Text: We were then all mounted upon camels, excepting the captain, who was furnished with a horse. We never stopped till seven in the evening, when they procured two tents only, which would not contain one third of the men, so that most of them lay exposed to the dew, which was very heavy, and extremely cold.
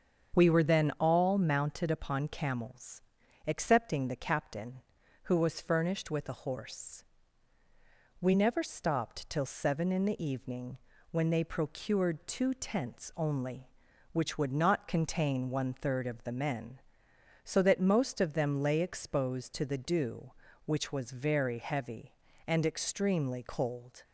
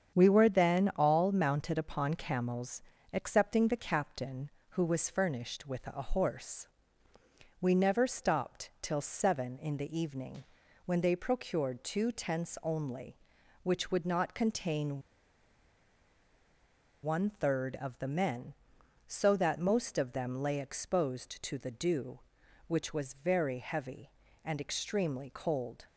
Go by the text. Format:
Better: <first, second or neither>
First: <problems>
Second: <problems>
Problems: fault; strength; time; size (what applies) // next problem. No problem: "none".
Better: first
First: starts louder than the rest; strong; until 1.4 s; 7 dB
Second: starts louder than the rest; strong; until 1.2 s; 7.5 dB // pauses between "contain" and "one"; strong; at 15.0 s; 2.0 s long